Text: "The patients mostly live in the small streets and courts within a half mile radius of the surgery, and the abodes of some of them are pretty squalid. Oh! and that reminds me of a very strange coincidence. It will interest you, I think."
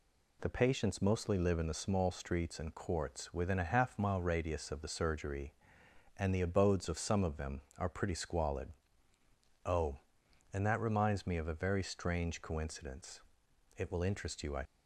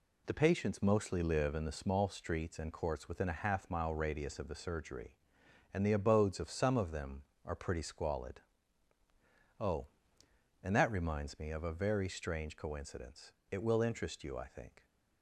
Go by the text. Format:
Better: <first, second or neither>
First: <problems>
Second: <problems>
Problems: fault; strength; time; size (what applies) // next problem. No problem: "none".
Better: second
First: stops before "think"; at 14.6 s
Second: none